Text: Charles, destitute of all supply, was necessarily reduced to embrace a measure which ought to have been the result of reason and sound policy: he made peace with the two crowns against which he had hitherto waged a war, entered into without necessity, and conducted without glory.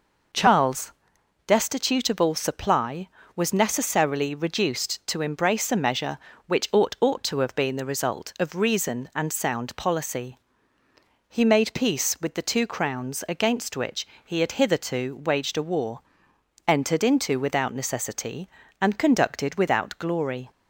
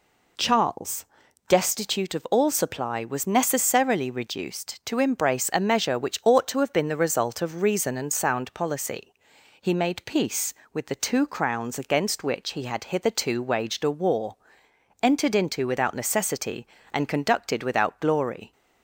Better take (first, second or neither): second